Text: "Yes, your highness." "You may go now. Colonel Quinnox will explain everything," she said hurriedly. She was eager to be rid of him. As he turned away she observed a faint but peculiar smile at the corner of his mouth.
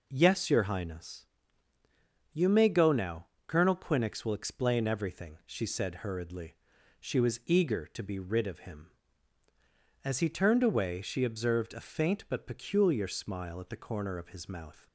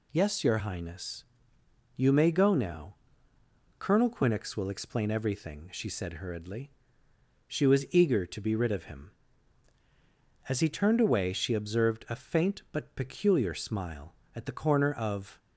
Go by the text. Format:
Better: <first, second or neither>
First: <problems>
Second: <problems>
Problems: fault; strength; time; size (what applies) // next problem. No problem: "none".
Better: first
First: none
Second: stops before "his mouth"; at 15.3 s